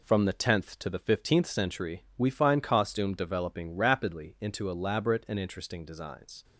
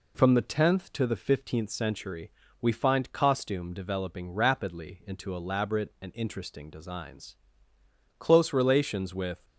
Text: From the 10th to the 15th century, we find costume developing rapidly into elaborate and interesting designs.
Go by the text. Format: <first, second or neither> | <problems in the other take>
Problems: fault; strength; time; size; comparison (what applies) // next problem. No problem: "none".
first | goes on to say "Close relations with"; noticeable; from 8.1 s on; 1.2 s long